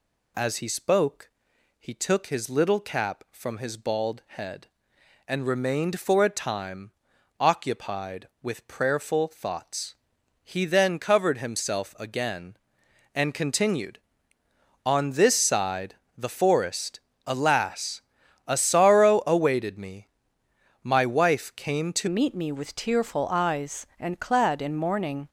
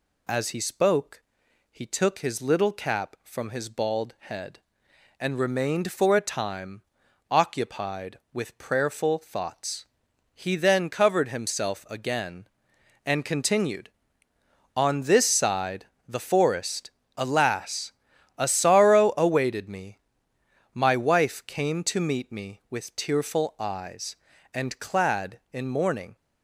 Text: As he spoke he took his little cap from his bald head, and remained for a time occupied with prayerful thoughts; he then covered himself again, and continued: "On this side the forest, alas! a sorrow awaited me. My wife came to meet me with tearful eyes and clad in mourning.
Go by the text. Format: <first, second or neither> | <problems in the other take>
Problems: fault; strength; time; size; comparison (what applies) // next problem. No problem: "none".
second | pauses between "spoke" and "he"; noticeable; at 1.3 s; 0.48 s long; noticeable in the second // pauses between "time" and "occupied"; noticeable; at 6.9 s; 0.48 s long; noticeable in the second // pauses between "side" and "the"; slight; at 15.9 s; 0.22 s long; slight in the second // changes voice at "meet"; from 22.0 s on; 3.2 s long